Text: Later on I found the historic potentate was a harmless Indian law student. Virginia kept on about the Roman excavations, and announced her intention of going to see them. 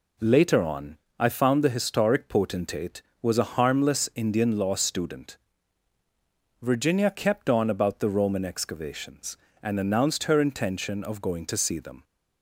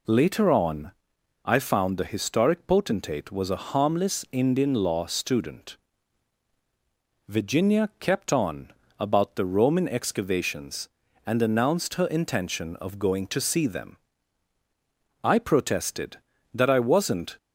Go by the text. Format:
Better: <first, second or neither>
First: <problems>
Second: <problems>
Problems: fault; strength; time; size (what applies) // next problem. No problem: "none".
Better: first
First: pauses between "on" and "I"; slight; at 0.9 s; 0.22 s long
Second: pauses between "on" and "I"; noticeable; at 0.9 s; 0.54 s long // pauses between "on" and "about"; slight; at 8.7 s; 0.26 s long // goes on to say "I protested that I wasn't"; strong; from 15.2 s on; 2.1 s long